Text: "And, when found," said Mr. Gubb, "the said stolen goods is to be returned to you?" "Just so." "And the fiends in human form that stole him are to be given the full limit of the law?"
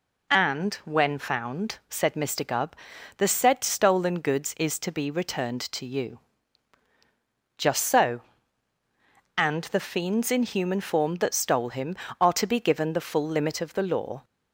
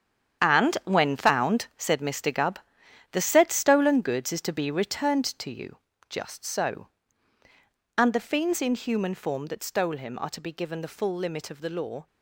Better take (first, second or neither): first